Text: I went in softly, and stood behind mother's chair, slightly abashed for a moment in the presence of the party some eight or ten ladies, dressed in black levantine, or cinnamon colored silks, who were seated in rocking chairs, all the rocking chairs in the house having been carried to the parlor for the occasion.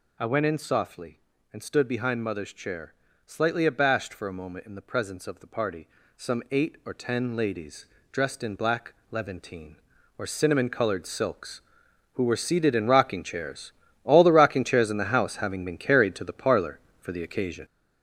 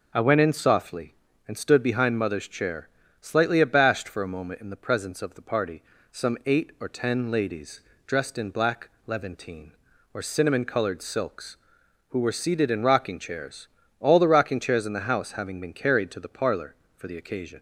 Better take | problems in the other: second | gets louder; throughout; 6.5 dB // pauses between "party" and "some"; slight; at 5.8 s; 0.28 s long; slight in the second // pauses between "black" and "levantine"; slight; at 8.9 s; 0.16 s long; slight in the second

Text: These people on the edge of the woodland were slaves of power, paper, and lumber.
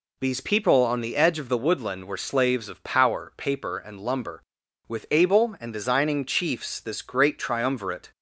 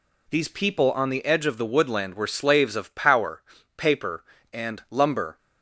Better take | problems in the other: second | goes on to say "With able and designing chiefs this great triumvirate"; strong; from 4.8 s on; 3.2 s long

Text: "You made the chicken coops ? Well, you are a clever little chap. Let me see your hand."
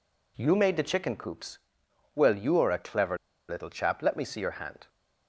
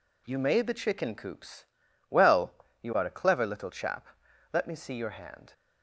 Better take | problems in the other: second | pauses between "clever" and "little"; slight; at 3.1 s; 0.32 s long

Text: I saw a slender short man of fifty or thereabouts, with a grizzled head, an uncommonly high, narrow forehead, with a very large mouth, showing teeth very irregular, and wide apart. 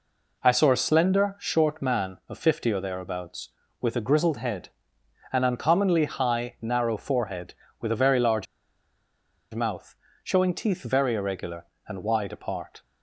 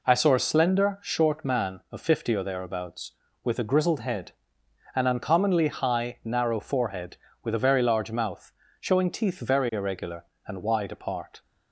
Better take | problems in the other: second | pauses between "large" and "mouth"; at 8.4 s; 1.0 s long

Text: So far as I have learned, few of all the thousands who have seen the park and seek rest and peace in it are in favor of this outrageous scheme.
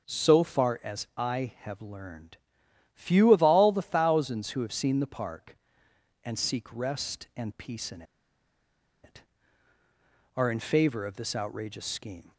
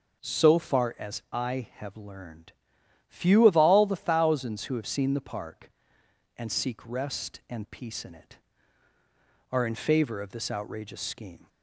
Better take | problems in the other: second | pauses between "in" and "it"; at 8.0 s; 1.0 s long

